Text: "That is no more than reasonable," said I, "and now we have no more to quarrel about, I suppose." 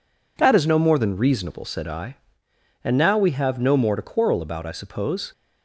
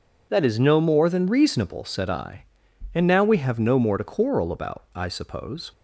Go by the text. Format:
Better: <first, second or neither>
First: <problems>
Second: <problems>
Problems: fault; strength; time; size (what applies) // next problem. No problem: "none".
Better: neither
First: none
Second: none